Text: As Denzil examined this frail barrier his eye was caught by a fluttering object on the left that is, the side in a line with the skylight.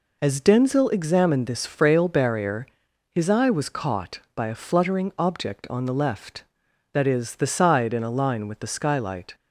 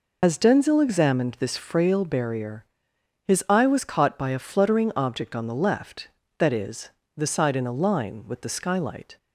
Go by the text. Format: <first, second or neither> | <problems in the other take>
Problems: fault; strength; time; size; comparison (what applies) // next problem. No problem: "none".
first | loses the start of "As"; at 0.2 s; 80 ms // pauses between "barrier" and "his"; noticeable; at 2.6 s; 0.60 s long; noticeable in the first